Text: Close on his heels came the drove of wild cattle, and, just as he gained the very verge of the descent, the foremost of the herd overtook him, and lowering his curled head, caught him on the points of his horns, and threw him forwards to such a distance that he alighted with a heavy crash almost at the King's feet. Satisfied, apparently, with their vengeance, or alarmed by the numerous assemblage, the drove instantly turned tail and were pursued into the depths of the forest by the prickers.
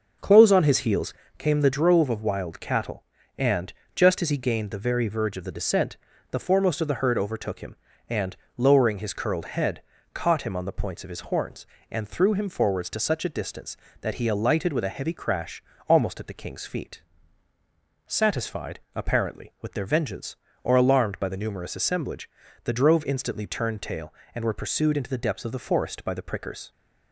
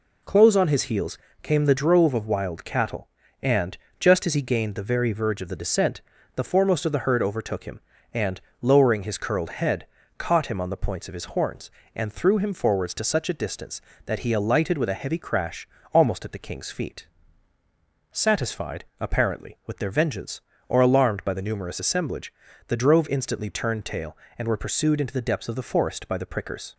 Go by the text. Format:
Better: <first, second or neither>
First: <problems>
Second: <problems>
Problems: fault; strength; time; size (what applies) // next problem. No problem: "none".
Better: second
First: starts louder than the rest; noticeable; until 1.4 s; 6 dB // pauses between "heels" and "came"; slight; at 1.1 s; 0.26 s long // pauses between "and" and "lowering"; slight; at 8.3 s; 0.20 s long // pauses between "crash" and "almost"; slight; at 15.6 s; 0.26 s long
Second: pauses between "heels" and "came"; slight; at 1.1 s; 0.26 s long // pauses between "and" and "lowering"; slight; at 8.4 s; 0.20 s long // pauses between "crash" and "almost"; slight; at 15.6 s; 0.26 s long